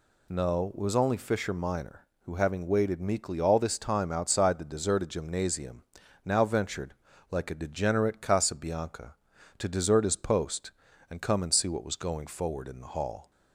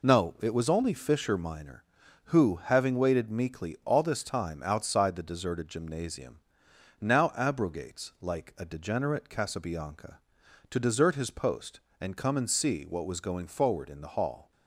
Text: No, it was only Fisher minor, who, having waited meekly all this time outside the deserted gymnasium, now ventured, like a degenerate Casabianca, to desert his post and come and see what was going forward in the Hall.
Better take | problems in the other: first | says "abrogates" for "ventured"; at 7.3 s

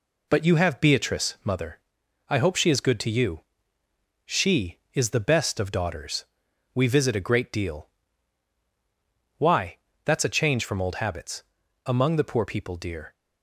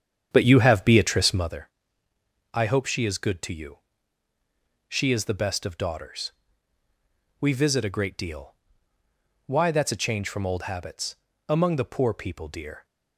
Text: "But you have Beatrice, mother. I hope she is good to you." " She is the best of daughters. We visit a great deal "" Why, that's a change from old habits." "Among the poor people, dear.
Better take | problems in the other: first | starts louder than the rest; strong; until 1.5 s; 8.5 dB

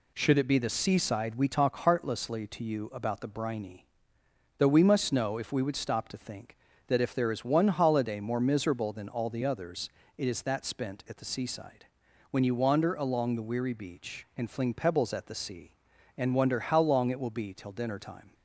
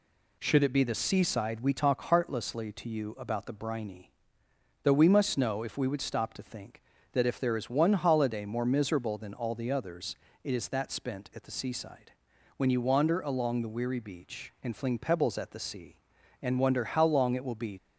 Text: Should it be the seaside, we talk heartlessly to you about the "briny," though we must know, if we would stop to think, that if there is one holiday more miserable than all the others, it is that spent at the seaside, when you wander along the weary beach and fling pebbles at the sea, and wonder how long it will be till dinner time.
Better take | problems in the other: first | stops before "till dinner time"; at 17.7 s

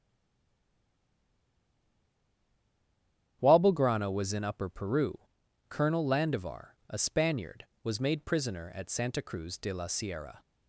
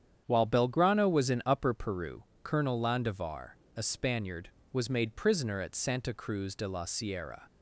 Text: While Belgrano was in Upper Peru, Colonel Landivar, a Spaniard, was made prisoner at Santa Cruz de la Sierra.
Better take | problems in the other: second | stays silent before the first word; strong; until 3.4 s; 3.4 s long // starts louder than the rest; strong; until 4.4 s; 9.5 dB; strong in the second

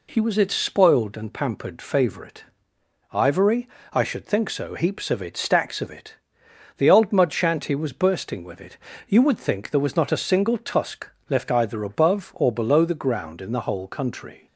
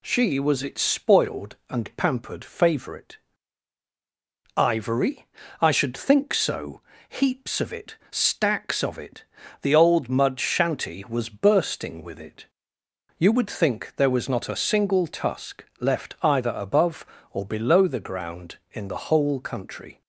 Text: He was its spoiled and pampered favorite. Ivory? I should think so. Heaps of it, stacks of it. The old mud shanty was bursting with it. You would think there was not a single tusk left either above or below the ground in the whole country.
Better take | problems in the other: first | says "She" for "He"; at 0.0 s // pauses between "tusk" and "left"; slight; at 15.6 s; 0.16 s long; slight in the first

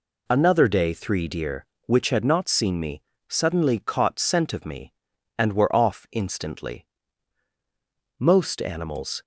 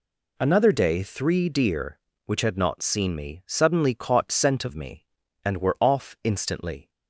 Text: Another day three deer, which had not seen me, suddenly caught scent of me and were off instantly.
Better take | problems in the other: second | goes on to say "Most animals"; noticeable; from 8.1 s on; 1.0 s long

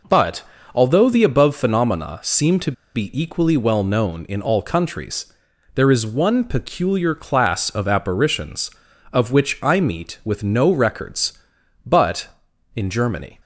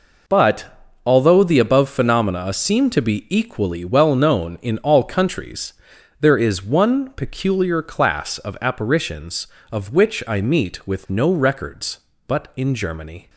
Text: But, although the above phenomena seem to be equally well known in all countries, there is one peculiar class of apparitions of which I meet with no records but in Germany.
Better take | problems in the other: second | pauses between "to" and "be"; slight; at 2.7 s; 0.22 s long

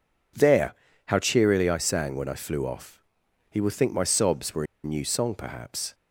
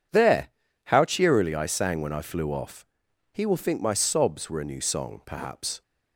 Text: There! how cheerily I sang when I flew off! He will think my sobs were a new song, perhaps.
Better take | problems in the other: second | pauses between "were" and "a"; slight; at 4.6 s; 0.19 s long

